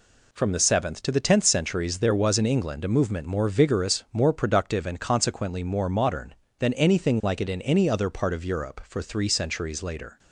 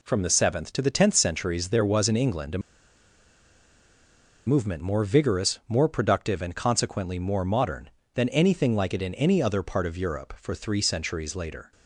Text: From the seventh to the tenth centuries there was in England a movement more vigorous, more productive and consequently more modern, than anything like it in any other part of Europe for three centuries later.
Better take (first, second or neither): first